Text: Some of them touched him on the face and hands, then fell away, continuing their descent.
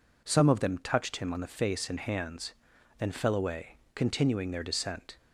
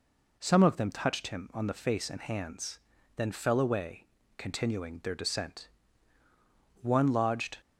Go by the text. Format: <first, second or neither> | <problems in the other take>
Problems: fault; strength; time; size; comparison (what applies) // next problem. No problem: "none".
first | goes on to say "One lodged"; noticeable; from 6.8 s on; 0.76 s long